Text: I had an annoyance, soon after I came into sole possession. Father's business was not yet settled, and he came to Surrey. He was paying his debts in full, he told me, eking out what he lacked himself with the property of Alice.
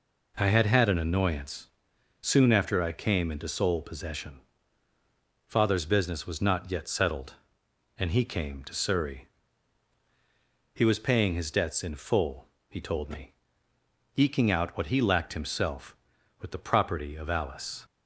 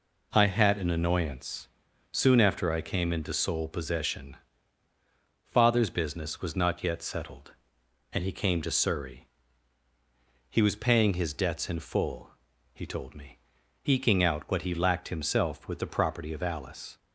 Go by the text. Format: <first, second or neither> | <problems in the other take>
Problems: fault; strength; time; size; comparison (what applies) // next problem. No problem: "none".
second | says "had" twice; at 0.6 s